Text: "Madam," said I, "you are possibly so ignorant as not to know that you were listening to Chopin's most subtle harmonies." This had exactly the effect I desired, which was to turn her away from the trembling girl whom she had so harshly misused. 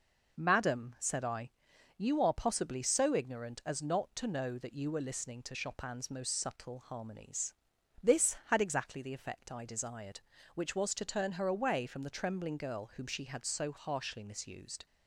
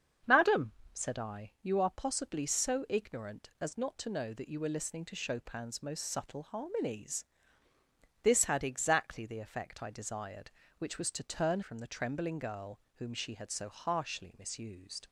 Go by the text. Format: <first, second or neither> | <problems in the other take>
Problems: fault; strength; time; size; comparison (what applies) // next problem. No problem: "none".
first | starts louder than the rest; strong; until 1.4 s; 7 dB // skips "her away"; at 11.6 s // pauses between "girl" and "whom"; slight; at 12.8 s; 0.16 s long